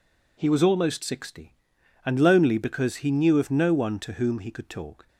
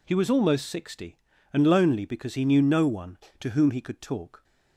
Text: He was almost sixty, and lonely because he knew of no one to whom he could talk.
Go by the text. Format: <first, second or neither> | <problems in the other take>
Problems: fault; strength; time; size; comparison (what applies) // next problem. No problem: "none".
first | skips "of"; at 2.6 s